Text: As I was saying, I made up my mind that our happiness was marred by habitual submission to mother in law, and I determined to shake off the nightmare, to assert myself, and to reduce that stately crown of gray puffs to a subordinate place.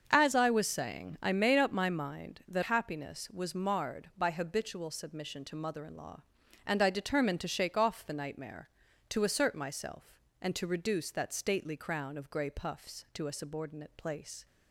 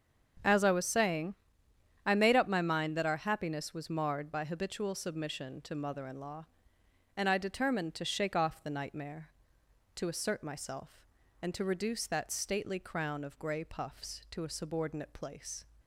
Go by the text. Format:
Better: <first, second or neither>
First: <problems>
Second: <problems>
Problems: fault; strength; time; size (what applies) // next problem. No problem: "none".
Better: second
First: starts louder than the rest; until 1.1 s; 7 dB // skips "our"; at 2.6 s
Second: starts louder than the rest; strong; until 2.1 s; 7.5 dB